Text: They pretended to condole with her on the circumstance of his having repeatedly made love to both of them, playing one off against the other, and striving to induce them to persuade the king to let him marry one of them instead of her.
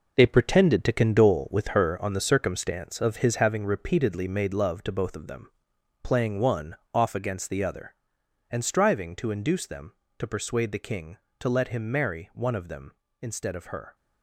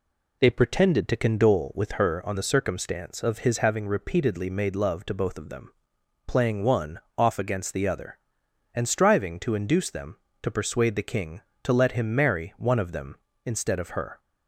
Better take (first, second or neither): second